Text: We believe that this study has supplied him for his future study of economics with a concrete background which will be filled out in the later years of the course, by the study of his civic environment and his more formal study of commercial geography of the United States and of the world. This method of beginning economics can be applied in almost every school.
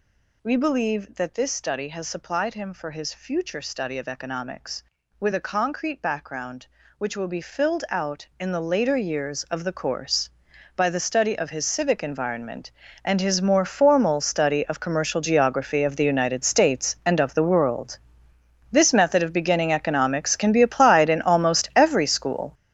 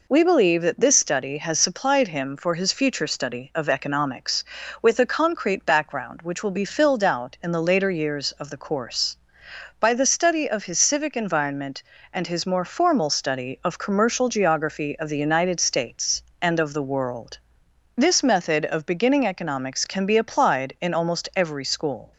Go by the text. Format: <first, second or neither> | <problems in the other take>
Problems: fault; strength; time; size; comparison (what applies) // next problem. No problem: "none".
second | gets louder; strong; throughout; 11.5 dB